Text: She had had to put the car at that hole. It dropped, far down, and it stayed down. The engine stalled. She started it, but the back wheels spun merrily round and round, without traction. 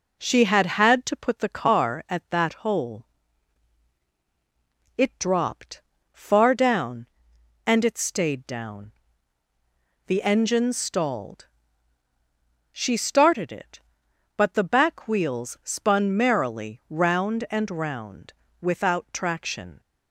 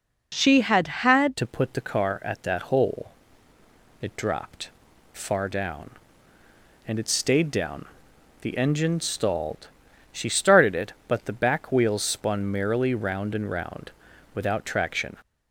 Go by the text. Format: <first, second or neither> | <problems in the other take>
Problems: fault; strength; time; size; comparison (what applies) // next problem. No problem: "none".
first | changes voice at "to"; from 1.3 s on; 13.8 s long